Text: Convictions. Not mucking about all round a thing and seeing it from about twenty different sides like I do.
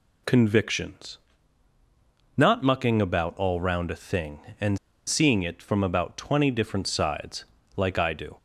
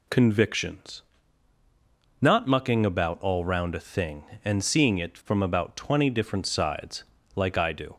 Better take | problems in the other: second | pauses between "and" and "seeing"; slight; at 4.7 s; 0.29 s long // pauses between "sides" and "like"; slight; at 7.4 s; 0.32 s long; slight in the second

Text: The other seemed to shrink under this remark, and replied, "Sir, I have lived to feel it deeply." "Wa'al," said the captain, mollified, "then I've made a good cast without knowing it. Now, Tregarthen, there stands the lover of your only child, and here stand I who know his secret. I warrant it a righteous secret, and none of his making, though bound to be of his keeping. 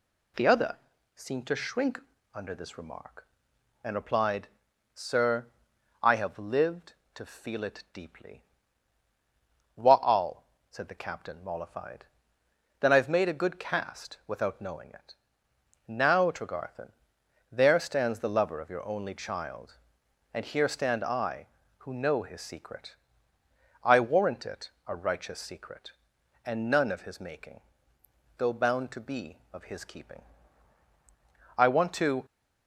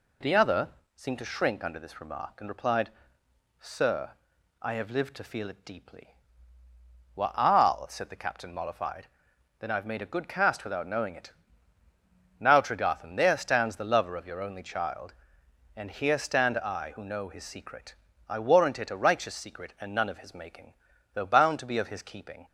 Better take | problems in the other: second | pauses between "other" and "seemed"; at 0.7 s; 0.40 s long; slight in the second // pauses between "shrink" and "under"; slight; at 1.9 s; 0.34 s long // goes on to say "I want to"; noticeable; from 31.5 s on; 0.68 s long

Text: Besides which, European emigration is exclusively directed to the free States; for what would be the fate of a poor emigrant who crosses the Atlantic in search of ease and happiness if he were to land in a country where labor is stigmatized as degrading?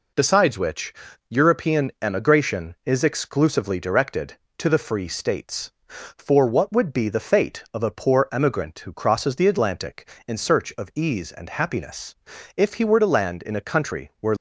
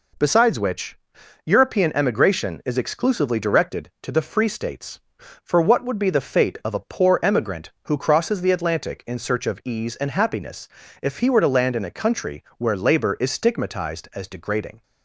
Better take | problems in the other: second | pauses between "happiness" and "if"; at 12.1 s; 0.42 s long; slight in the second // stops before "labor is stigmatized as degrading"; at 14.3 s

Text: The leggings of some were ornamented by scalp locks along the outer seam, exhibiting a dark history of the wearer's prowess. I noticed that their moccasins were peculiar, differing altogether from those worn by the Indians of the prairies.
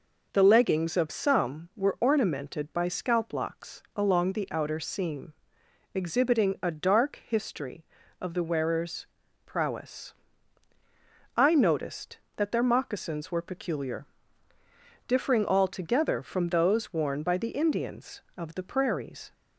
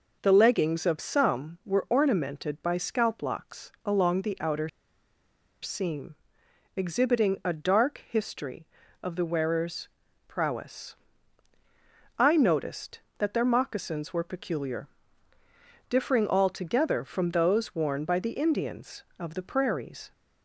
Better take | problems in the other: first | pauses between "outer" and "seam"; noticeable; at 4.6 s; 0.95 s long // pauses between "wearer's" and "prowess"; slight; at 9.8 s; 0.36 s long; slight in the first

